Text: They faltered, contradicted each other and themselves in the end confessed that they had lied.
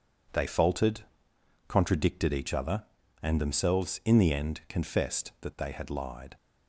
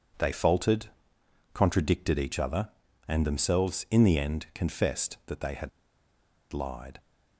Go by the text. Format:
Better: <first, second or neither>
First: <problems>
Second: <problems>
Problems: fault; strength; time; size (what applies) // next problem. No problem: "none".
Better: first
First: none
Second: pauses between "had" and "lied"; noticeable; at 5.6 s; 0.83 s long